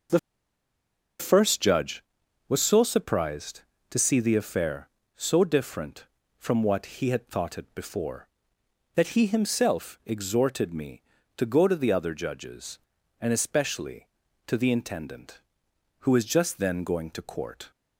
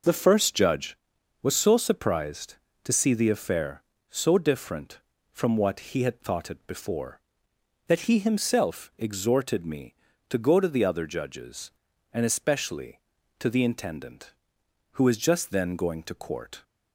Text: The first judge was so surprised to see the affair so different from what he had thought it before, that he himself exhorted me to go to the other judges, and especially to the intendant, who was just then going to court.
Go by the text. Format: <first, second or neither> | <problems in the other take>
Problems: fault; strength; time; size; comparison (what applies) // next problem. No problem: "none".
second | pauses between "The" and "first"; at 0.1 s; 1.0 s long